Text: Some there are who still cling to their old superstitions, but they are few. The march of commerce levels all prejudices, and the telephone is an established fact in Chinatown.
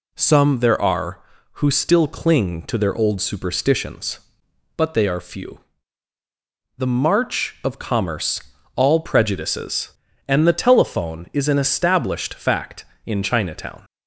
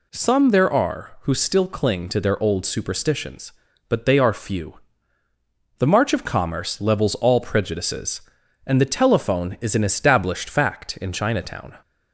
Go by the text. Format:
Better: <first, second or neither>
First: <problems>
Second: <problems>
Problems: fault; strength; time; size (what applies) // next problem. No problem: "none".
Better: second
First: skips "levels"; at 8.5 s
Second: none